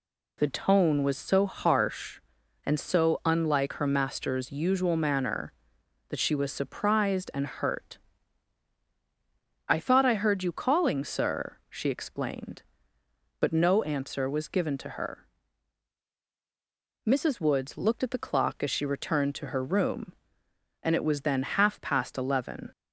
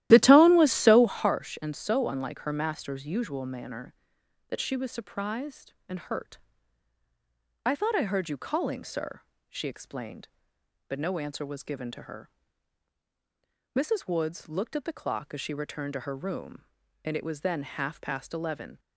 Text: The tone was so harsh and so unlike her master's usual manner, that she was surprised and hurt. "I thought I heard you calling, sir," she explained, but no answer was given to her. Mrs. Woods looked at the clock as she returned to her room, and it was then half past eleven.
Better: first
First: none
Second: starts louder than the rest; strong; until 1.3 s; 14 dB

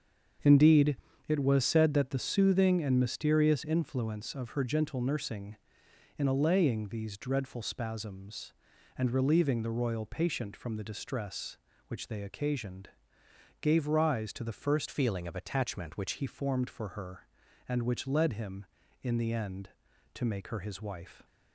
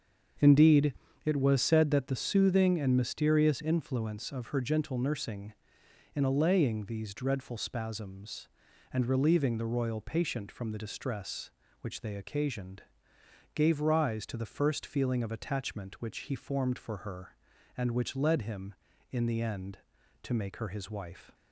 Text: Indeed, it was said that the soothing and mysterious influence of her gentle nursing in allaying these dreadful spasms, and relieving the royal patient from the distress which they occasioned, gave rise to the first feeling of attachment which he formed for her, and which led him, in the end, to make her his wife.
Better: second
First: starts louder than the rest; until 1.7 s; 7 dB // changes voice from "feeling" to "which"; from 14.9 to 16.1 s; 1.2 s long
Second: starts louder than the rest; until 1.7 s; 7 dB

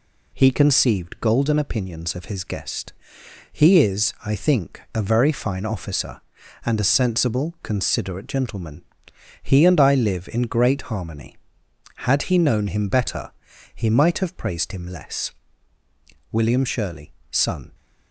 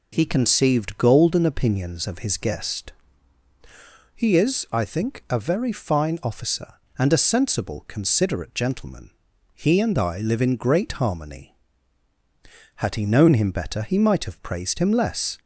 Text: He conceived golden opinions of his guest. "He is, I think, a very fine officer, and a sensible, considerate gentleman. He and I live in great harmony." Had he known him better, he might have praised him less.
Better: second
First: goes on to say "William Shirley son"; from 16.3 s on; 1.4 s long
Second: none

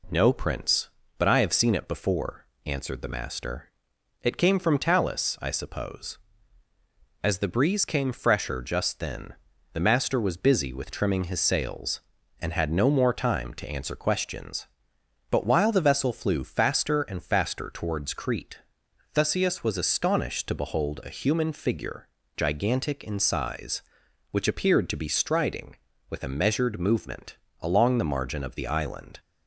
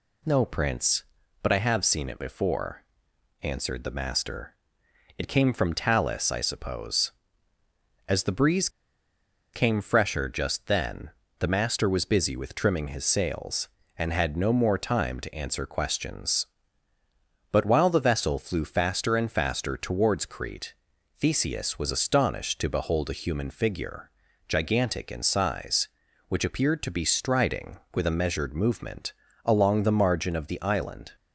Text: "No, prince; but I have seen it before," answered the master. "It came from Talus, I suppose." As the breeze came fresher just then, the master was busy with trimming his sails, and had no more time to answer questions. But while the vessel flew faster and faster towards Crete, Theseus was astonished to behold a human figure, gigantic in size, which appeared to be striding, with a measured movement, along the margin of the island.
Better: first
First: none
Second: pauses between "breeze" and "came"; noticeable; at 8.6 s; 0.84 s long

